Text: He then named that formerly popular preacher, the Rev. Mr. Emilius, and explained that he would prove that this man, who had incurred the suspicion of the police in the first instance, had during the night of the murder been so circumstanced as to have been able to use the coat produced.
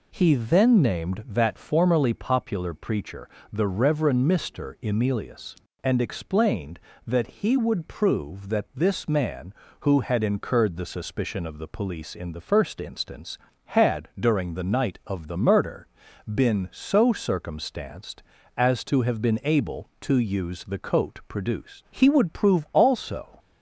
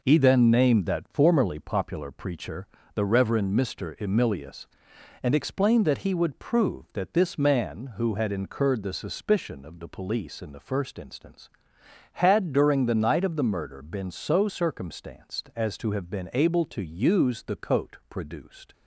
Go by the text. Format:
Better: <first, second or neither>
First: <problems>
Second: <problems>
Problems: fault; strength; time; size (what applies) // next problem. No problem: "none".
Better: second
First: pauses between "murder" and "been"; noticeable; at 15.8 s; 0.48 s long // goes on to say "He would prove also"; from 21.9 s on; 1.4 s long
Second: none